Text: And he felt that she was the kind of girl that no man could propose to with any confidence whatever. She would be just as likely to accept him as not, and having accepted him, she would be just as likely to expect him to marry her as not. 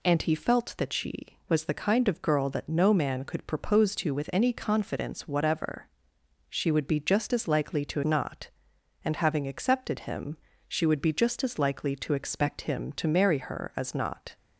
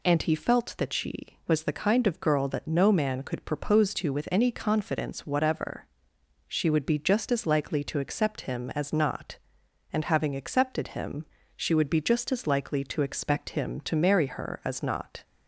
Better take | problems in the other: second | skips "accept him as"; at 8.0 s

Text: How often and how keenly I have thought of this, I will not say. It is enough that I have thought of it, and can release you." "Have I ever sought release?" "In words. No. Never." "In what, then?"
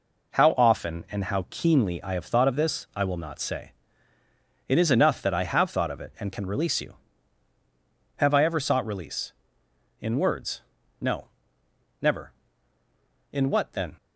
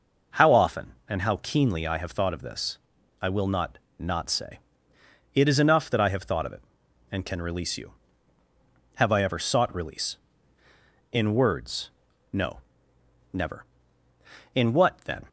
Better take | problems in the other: first | says "not" twice; at 3.9 s

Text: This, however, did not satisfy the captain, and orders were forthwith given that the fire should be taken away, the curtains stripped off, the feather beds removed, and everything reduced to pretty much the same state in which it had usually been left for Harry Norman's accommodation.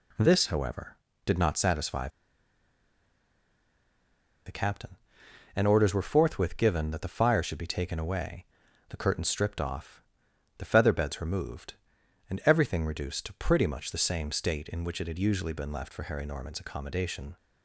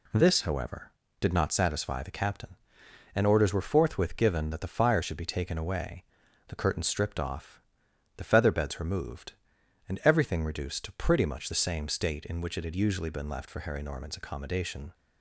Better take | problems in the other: second | pauses between "satisfy" and "the"; strong; at 2.0 s; 2.3 s long

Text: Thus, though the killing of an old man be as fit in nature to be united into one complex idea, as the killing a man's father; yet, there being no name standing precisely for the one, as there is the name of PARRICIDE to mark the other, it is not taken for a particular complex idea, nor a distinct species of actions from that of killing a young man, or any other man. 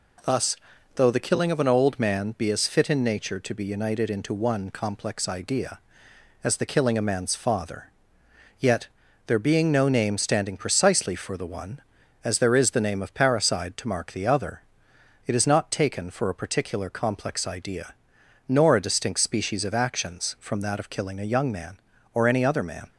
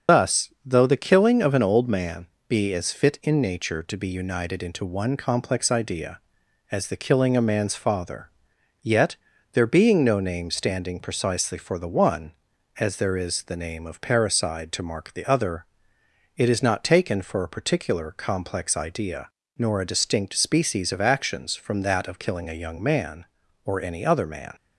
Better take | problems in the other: first | loses the start of "Thus"; at 0.0 s; 100 ms // starts louder than the rest; until 1.2 s; 6.5 dB // pauses between "man" and "be"; slight; at 2.2 s; 0.22 s long

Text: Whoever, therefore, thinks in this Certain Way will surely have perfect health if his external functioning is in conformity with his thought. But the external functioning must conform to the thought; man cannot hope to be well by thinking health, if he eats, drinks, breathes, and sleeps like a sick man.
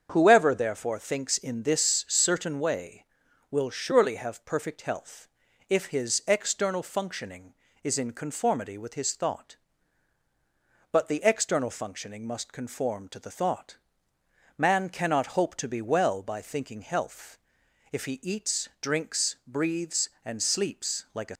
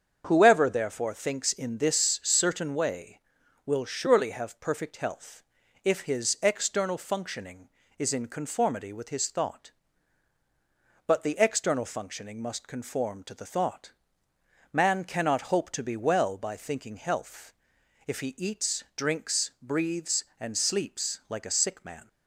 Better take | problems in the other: second | starts louder than the rest; strong; until 1.1 s; 7 dB; strong in the second // pauses between "health" and "if"; at 5.2 s; 0.40 s long; also in the second // stops before "sick man"; at 21.3 s

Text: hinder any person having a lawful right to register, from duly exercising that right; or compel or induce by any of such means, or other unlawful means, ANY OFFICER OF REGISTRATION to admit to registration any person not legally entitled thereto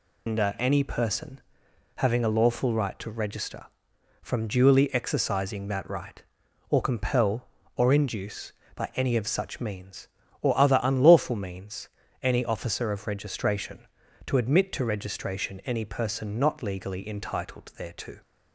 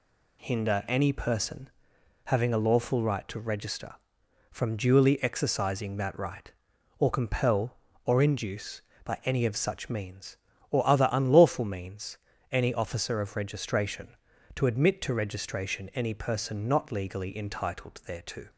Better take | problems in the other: second | loses the start of "hinder"; at 0.2 s; 155 ms // pauses between "person" and "having"; noticeable; at 1.3 s; 0.56 s long; noticeable in the second

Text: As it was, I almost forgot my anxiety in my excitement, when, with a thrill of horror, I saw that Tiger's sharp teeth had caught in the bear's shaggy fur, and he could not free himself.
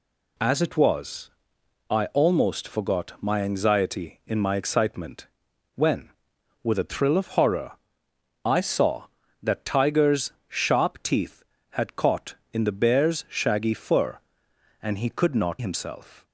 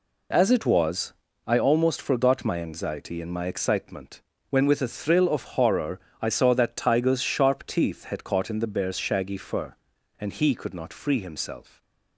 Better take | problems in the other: second | skips "free"; at 15.5 s

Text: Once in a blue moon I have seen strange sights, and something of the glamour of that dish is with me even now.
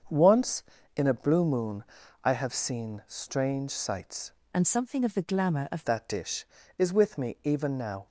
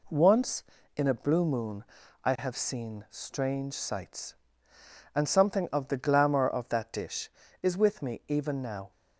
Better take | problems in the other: second | starts louder than the rest; until 1.4 s; 7 dB // pauses between "moon" and "I"; at 1.8 s; 0.42 s long; also in the second // changes voice from "and" to "of"; from 4.5 to 5.8 s; 1.3 s long

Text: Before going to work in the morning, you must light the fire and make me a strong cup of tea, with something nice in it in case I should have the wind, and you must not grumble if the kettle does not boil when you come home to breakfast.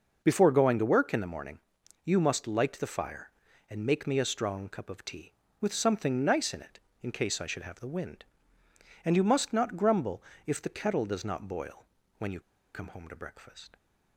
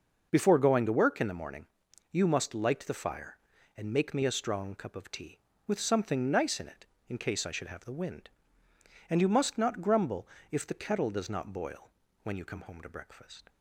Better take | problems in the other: second | pauses between "grumble" and "if"; slight; at 10.2 s; 0.24 s long; slight in the second // pauses between "boil" and "when"; slight; at 11.8 s; 0.34 s long; slight in the second // pauses between "you" and "come"; slight; at 12.4 s; 0.33 s long

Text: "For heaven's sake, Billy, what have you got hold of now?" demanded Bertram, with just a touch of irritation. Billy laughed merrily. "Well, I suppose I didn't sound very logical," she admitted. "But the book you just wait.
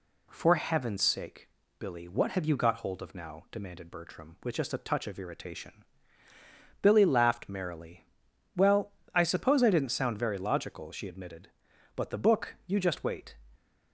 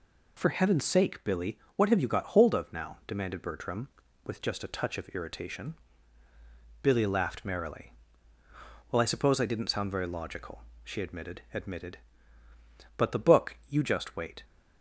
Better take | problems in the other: first | says "admitted" twice; at 11.5 s

